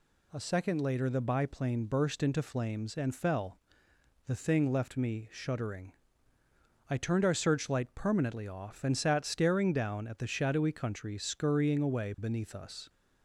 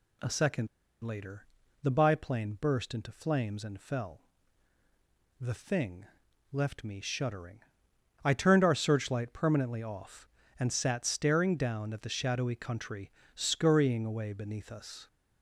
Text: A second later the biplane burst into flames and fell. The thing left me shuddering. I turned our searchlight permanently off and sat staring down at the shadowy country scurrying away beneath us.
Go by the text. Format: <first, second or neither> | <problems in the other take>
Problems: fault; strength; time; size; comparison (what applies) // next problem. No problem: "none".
first | pauses between "second" and "later"; slight; at 0.6 s; 0.35 s long // pauses between "later" and "the"; at 1.4 s; 0.38 s long // pauses between "thing" and "left"; noticeable; at 6.0 s; 0.46 s long // pauses between "country" and "scurrying"; slight; at 13.1 s; 0.22 s long